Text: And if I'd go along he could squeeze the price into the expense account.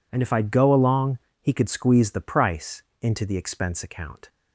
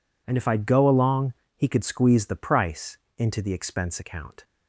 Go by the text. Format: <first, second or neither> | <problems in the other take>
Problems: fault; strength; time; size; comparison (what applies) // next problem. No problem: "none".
neither | pauses between "along" and "he"; slight; the same in both // pauses between "price" and "into"; slight; the same in both